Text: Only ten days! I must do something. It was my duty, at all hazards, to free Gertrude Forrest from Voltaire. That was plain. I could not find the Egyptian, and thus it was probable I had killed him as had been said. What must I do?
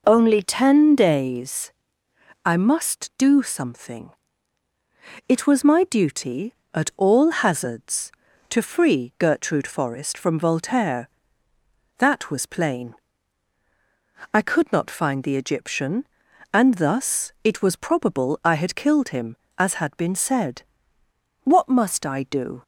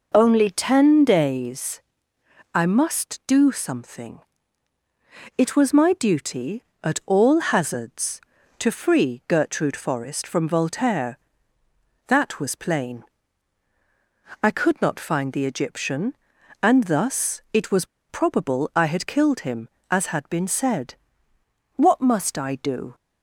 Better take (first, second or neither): first